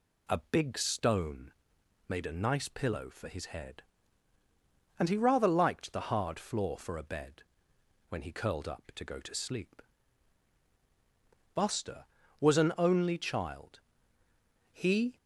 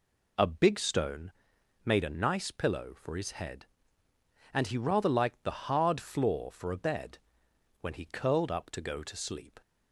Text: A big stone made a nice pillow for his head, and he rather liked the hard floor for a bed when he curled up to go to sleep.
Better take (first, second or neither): second